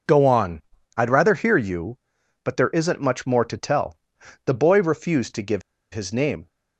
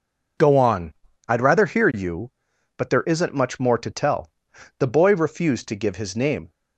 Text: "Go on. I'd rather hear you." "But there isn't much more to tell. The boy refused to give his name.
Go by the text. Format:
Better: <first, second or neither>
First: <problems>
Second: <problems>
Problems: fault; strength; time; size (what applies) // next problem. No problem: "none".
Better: second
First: pauses between "give" and "his"; slight; at 5.6 s; 0.32 s long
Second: none